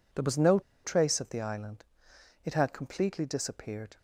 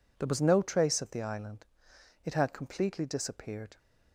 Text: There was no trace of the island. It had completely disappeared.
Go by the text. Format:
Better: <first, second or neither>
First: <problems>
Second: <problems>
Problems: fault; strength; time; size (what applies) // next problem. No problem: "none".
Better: second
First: pauses between "no" and "trace"; slight; at 0.5 s; 0.25 s long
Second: none